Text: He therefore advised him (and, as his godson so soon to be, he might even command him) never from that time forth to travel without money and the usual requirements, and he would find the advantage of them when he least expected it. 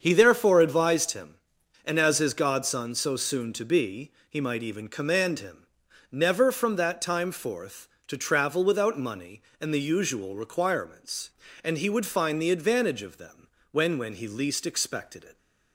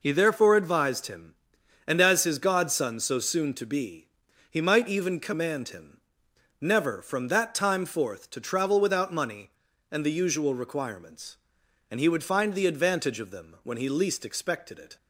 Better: second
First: starts louder than the rest; until 1.0 s; 7 dB // pauses between "them" and "when"; slight; at 13.4 s; 0.26 s long // says "when" twice; at 13.9 s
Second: none

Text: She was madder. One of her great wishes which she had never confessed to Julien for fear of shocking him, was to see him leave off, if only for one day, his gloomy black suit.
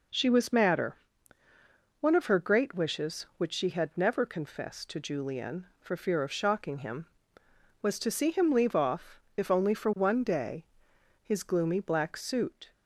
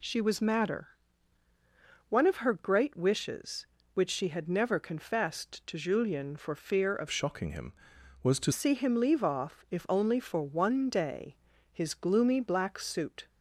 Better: first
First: none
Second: changes voice from "shocking" to "to"; from 7.0 to 8.5 s; 1.5 s long

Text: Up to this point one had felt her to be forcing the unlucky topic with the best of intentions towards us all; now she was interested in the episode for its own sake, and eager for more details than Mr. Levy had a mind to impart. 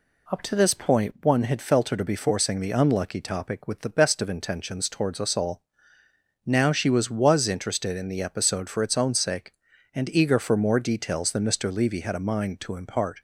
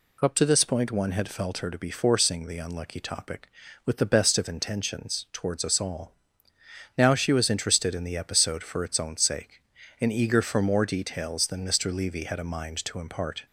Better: second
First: says "was" twice; at 7.0 s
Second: none

